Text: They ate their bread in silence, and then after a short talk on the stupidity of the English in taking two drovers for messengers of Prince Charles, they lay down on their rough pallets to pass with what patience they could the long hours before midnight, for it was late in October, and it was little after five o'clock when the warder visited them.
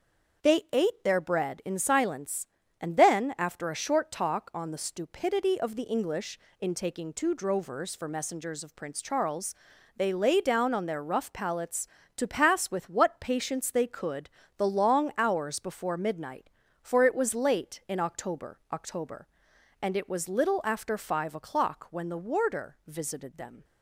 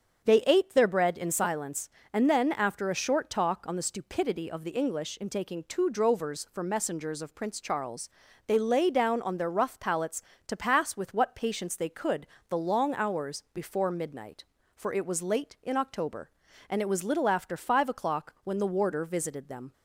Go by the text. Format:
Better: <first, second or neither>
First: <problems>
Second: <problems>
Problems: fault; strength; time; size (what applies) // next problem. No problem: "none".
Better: second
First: starts louder than the rest; until 1.5 s; 6.5 dB // pauses between "could" and "the"; slight; at 14.2 s; 0.26 s long // says "October" twice; at 18.7 s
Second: starts louder than the rest; strong; until 1.2 s; 7 dB // pauses between "could" and "the"; slight; at 12.2 s; 0.26 s long